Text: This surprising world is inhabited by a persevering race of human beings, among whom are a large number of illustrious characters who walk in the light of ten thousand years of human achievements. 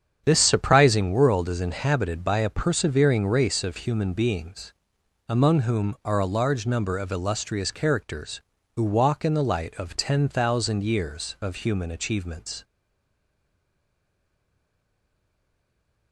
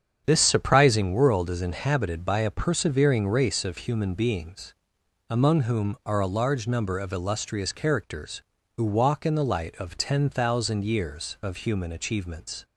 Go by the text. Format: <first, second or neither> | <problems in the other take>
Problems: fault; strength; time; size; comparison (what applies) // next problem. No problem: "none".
second | starts louder than the rest; strong; until 1.2 s; 8 dB; strong in the second // stays silent after the last word; strong; from 12.6 s on; 3.5 s long